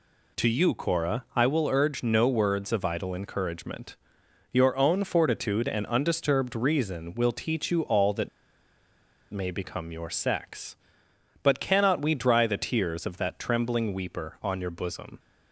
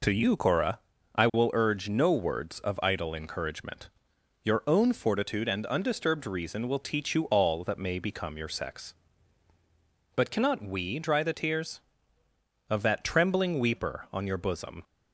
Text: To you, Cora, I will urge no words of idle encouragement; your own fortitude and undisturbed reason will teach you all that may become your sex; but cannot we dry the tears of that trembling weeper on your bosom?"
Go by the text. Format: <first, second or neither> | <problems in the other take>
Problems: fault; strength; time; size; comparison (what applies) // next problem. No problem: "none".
second | pauses between "that" and "may"; at 8.2 s; 1.0 s long